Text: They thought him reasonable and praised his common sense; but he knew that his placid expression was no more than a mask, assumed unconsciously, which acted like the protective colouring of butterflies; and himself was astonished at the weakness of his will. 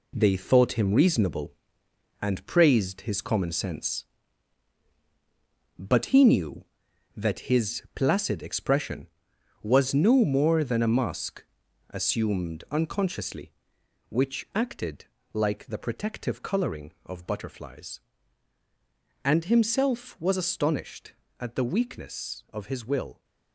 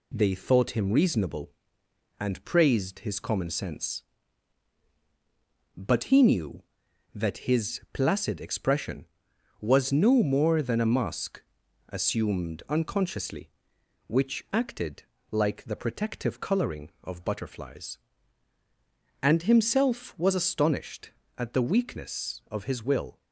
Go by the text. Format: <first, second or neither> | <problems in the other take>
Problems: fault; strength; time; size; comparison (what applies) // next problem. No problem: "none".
second | gets quieter; strong; throughout; 7 dB // pauses between "acted" and "like"; slight; at 15.0 s; 0.26 s long; slight in the second